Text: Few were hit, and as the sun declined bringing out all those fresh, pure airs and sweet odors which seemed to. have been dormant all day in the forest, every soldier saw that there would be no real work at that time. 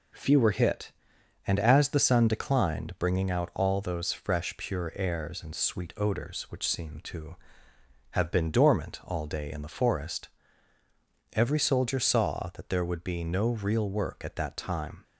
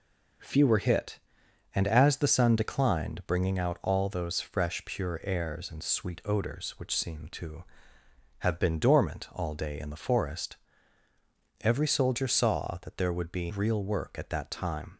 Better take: first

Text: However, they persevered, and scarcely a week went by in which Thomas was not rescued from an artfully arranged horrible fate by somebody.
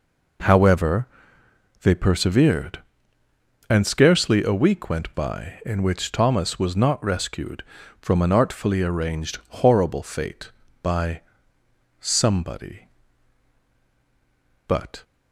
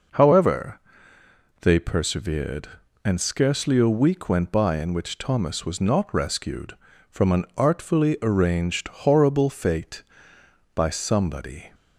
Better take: second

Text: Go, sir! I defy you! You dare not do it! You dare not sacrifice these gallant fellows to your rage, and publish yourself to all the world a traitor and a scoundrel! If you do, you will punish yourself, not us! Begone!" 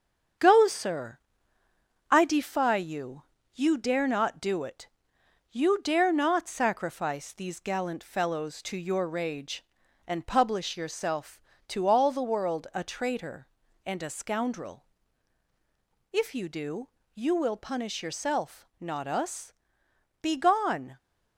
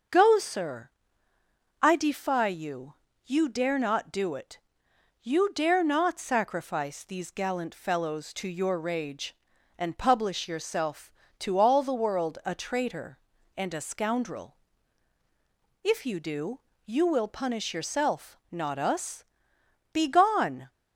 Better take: second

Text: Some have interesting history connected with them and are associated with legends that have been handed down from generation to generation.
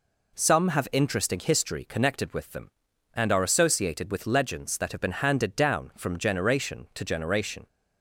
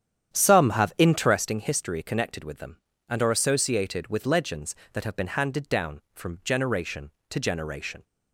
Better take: first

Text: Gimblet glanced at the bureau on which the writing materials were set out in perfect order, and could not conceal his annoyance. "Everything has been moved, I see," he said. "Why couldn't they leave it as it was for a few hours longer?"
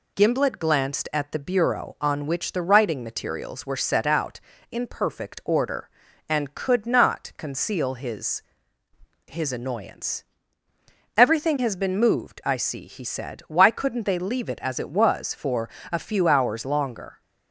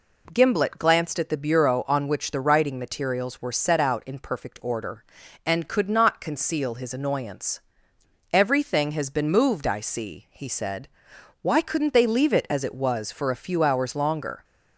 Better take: second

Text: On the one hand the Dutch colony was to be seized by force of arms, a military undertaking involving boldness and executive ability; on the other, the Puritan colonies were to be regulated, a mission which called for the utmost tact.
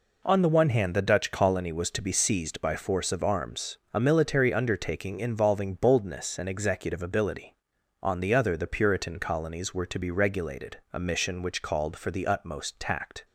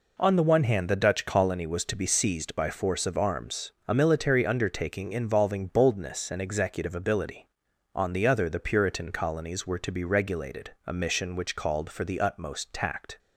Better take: neither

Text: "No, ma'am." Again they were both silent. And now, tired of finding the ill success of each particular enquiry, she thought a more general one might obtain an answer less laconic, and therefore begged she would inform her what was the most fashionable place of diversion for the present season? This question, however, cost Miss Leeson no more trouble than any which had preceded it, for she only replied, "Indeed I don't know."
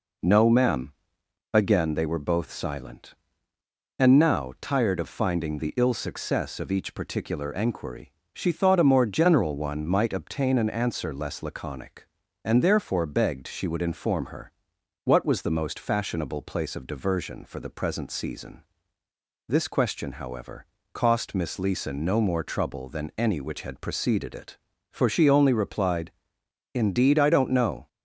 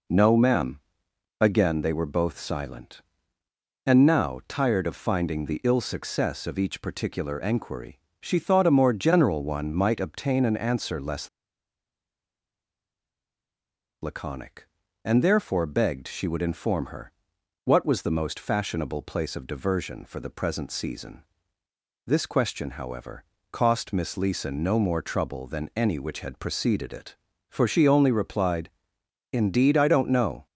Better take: first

